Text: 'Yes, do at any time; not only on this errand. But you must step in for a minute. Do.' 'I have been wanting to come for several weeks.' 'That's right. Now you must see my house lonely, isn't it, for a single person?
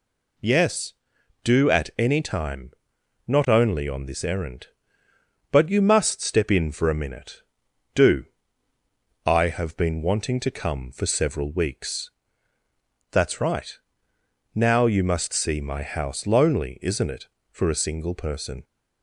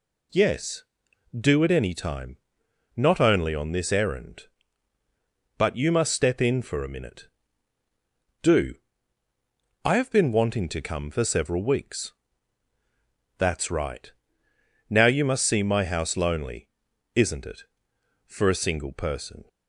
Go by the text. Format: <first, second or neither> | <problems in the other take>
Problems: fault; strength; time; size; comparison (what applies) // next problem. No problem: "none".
neither | none